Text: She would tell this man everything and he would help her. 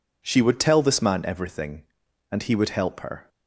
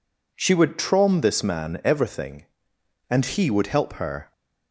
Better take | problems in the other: first | says "trom" for "tell"; at 0.7 s

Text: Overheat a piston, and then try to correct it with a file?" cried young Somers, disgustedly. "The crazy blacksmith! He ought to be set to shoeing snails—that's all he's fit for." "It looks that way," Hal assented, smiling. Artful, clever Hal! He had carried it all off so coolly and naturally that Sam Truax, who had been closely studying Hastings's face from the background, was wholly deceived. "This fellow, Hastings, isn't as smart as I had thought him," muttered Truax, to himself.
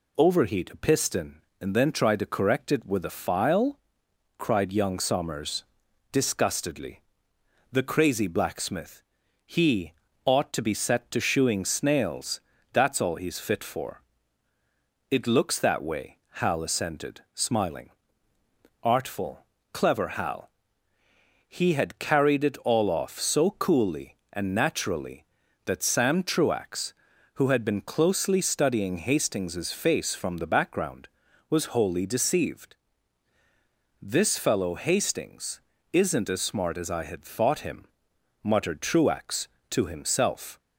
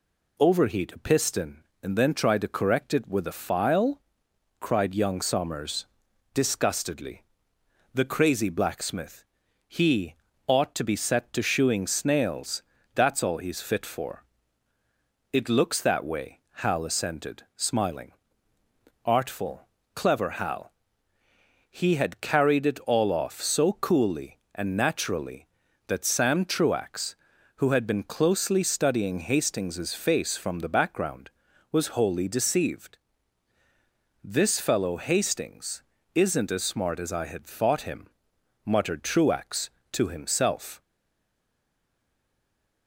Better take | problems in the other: first | pauses between "He" and "ought"; slight; at 10.1 s; 0.32 s long; slight in the first // stays silent after the last word; noticeable; from 40.8 s on; 2.0 s long

